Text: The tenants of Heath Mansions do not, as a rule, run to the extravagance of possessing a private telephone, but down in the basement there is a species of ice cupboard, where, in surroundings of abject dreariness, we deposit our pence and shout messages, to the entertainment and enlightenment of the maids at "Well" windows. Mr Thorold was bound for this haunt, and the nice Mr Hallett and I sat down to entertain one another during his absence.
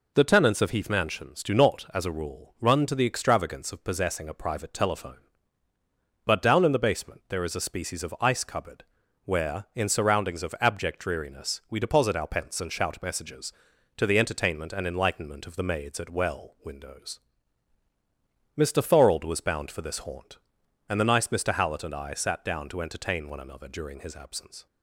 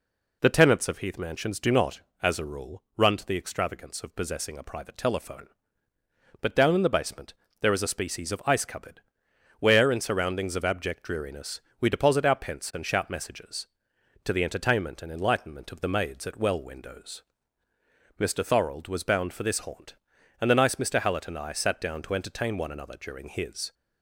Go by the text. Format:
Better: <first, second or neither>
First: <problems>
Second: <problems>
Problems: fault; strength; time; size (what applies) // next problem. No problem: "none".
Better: first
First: none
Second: pauses between "basement" and "there"; slight; at 7.3 s; 0.28 s long // stops before "absence"; at 23.7 s